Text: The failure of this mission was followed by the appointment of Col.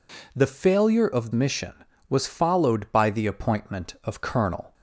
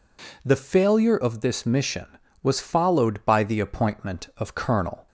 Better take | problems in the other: second | skips "this"; at 1.3 s

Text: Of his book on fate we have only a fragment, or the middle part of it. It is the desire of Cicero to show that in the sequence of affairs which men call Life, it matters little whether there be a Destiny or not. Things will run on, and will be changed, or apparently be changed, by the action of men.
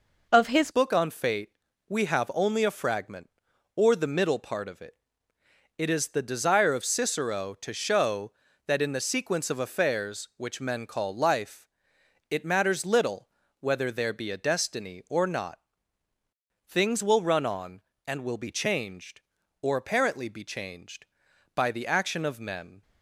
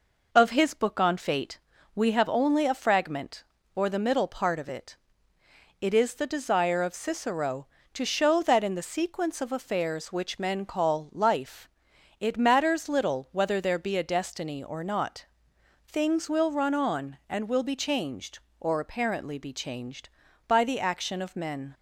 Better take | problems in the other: second | changes voice at "book"; from 0.7 s on; 22.1 s long // pauses between "fate" and "we"; slight; at 1.5 s; 0.36 s long; slight in the second // pauses between "little" and "whether"; slight; at 13.2 s; 0.32 s long

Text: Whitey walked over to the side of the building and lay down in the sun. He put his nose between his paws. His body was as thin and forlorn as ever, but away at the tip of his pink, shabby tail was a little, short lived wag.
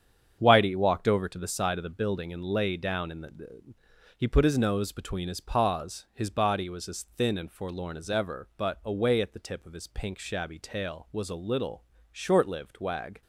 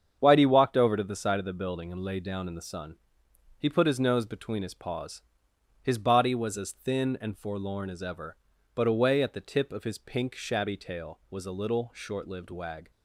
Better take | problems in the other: second | starts louder than the rest; strong; until 1.4 s; 7.5 dB; strong in the second // skips "sun"; at 3.7 s

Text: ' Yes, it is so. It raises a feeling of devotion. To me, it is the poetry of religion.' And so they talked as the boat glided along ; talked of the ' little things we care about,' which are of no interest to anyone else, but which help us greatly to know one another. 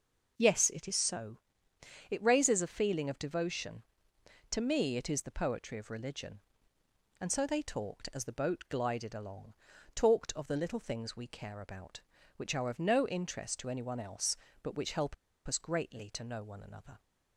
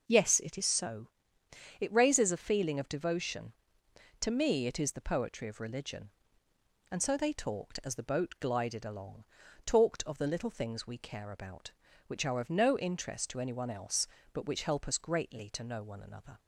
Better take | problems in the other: second | pauses between "help" and "us"; slight; at 15.1 s; 0.32 s long

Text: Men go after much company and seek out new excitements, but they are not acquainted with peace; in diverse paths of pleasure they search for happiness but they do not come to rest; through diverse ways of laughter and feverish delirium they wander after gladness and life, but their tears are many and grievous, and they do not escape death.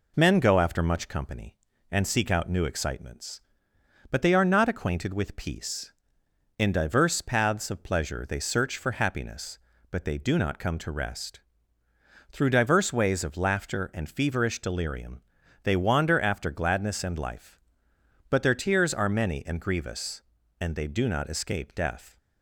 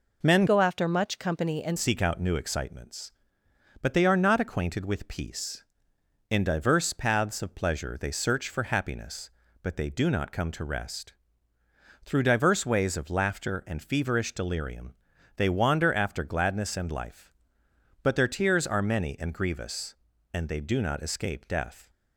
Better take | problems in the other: first | changes voice from "go" to "and"; from 0.4 to 1.7 s; 1.3 s long // pauses between "delirium" and "they"; at 14.9 s; 0.42 s long; also in the first

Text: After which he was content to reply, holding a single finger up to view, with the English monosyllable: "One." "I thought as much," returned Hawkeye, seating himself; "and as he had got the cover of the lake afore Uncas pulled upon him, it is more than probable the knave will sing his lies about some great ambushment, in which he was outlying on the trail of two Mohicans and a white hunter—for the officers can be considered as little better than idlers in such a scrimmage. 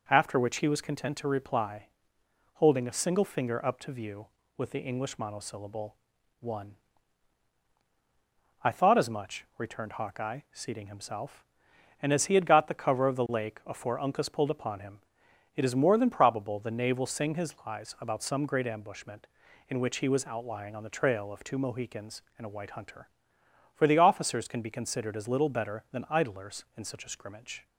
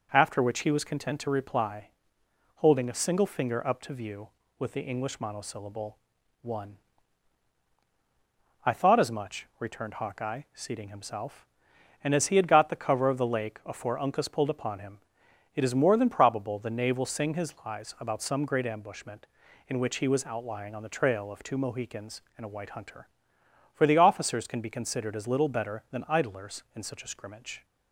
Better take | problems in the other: neither | none

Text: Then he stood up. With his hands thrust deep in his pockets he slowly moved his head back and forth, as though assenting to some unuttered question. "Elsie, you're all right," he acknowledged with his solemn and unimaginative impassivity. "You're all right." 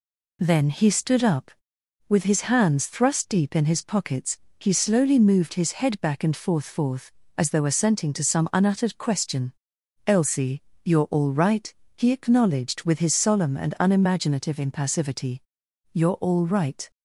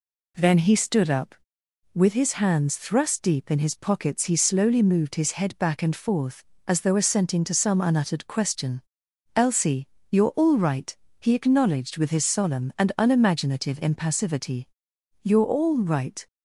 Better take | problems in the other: second | pauses between "pockets" and "he"; slight; at 4.3 s; 0.20 s long // says "forth" twice; at 6.6 s

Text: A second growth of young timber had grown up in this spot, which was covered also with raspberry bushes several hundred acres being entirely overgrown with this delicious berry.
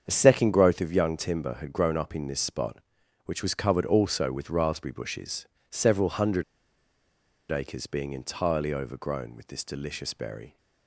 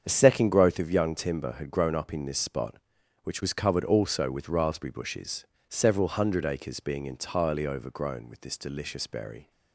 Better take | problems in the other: second | starts louder than the rest; strong; until 1.0 s; 7.5 dB; strong in the second // pauses between "bushes" and "several"; slight; at 5.4 s; 0.28 s long; slight in the second // pauses between "hundred" and "acres"; at 6.4 s; 1.0 s long

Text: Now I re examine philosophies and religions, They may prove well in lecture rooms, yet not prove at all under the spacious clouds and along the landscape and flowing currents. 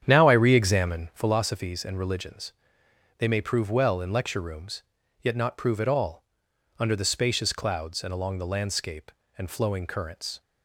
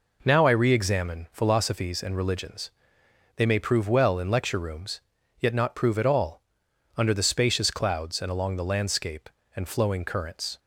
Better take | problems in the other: second | starts louder than the rest; strong; until 1.3 s; 9 dB // pauses between "all" and "under"; noticeable; at 6.2 s; 0.52 s long; noticeable in the second

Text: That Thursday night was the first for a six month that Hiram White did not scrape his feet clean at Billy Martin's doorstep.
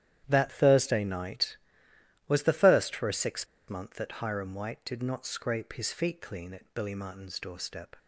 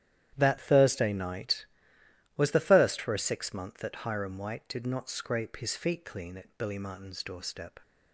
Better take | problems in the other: second | starts louder than the rest; strong; until 1.2 s; 11 dB; strong in the second // pauses between "six" and "month"; slight; at 3.4 s; 0.22 s long

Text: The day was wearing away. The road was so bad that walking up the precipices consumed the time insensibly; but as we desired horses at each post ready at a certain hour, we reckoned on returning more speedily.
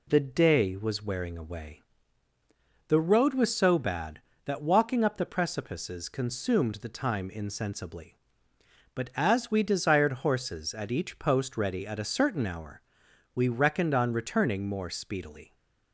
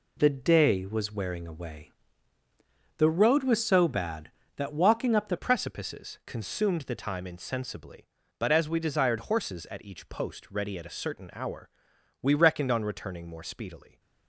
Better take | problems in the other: first | changes voice at "precipices"; from 5.3 s on; 8.6 s long

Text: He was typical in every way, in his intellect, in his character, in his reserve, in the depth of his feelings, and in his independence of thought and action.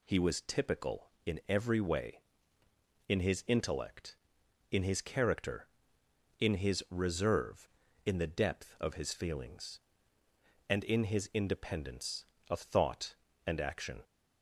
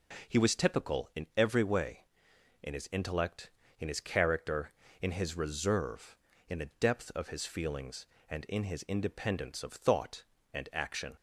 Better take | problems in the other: neither | none

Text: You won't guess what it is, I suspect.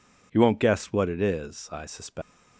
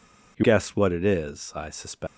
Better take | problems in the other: first | skips "won't"; at 0.4 s

